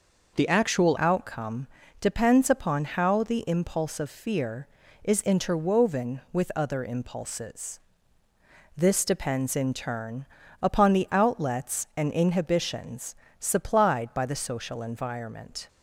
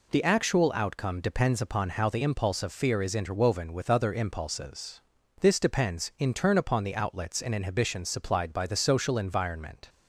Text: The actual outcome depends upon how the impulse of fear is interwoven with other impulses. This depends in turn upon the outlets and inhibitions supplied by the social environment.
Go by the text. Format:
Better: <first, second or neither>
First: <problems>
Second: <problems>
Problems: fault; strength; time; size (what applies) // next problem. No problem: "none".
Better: second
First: changes voice at "outcome"; from 0.9 s on; 14.7 s long // pauses between "outcome" and "depends"; slight; at 1.6 s; 0.32 s long // pauses between "turn" and "upon"; slight; at 10.2 s; 0.36 s long // pauses between "inhibitions" and "supplied"; slight; at 13.1 s; 0.24 s long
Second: none